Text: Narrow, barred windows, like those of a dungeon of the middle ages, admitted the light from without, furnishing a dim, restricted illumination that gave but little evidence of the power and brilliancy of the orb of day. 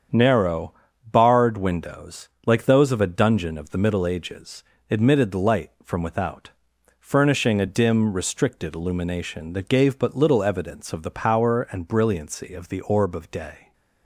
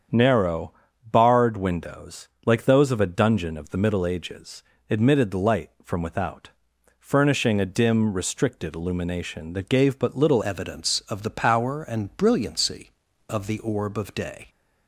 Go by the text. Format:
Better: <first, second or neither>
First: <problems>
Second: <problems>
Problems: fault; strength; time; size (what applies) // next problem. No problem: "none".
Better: first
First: starts louder than the rest; strong; until 1.4 s; 8 dB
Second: starts louder than the rest; strong; until 1.4 s; 8 dB // changes voice at "evidence"; from 10.4 s on; 4.0 s long